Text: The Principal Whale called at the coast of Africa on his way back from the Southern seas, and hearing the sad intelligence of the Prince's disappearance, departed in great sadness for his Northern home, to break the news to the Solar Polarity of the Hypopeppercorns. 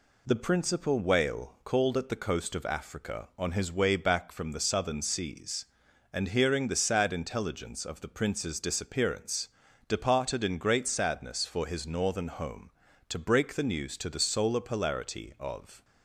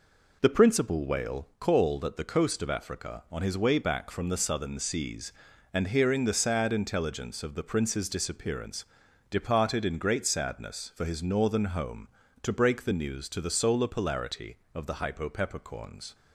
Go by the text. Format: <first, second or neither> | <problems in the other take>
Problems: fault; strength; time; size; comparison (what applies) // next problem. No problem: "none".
second | stops before "the Hypopeppercorns"; at 15.8 s